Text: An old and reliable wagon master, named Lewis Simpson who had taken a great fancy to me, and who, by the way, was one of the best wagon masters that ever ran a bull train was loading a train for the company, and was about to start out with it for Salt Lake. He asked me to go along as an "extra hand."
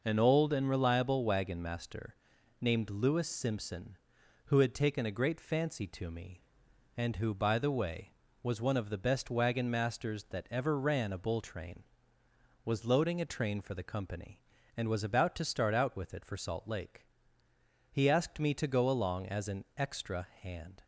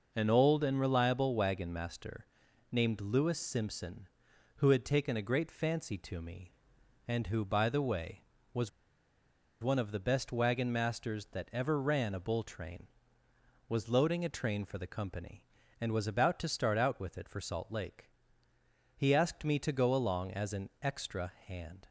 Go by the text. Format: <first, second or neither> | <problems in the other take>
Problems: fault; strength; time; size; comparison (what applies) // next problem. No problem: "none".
first | pauses between "was" and "one"; noticeable; at 8.6 s; 0.94 s long